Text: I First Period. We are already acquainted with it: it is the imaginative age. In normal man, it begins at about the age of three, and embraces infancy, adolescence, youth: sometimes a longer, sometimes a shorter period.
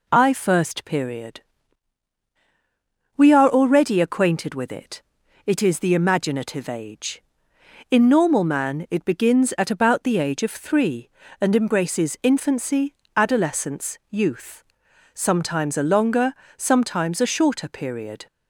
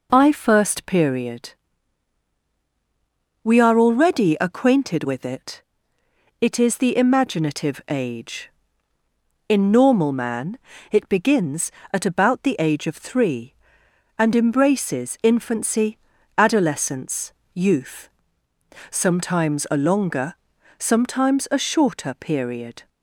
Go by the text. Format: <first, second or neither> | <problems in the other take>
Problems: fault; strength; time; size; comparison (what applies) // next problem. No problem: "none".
neither | none